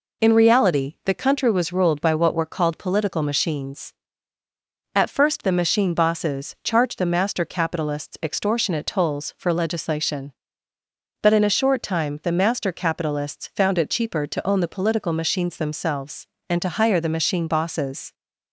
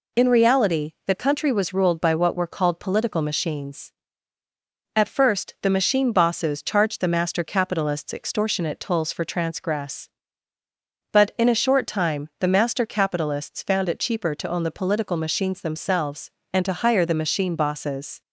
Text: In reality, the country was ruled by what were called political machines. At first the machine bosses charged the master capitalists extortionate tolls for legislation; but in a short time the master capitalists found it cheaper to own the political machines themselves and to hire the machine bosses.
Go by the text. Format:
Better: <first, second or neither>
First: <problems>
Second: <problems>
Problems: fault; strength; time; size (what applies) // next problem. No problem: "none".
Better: first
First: none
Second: says "transgress" for "legislation"; at 9.2 s